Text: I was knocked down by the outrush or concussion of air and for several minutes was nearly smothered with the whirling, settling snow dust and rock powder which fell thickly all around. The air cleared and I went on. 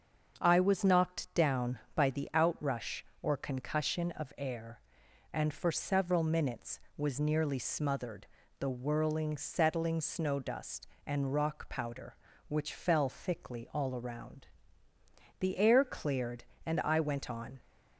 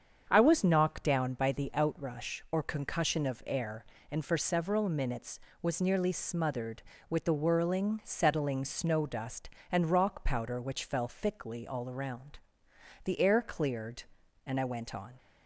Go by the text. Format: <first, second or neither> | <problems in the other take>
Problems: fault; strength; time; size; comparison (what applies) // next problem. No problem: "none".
second | starts louder than the rest; until 1.4 s; 6.5 dB; strong in the second // skips "with"; at 8.4 s